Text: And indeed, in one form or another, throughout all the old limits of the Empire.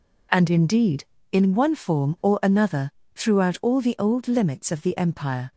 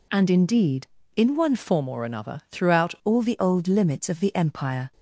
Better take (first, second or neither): first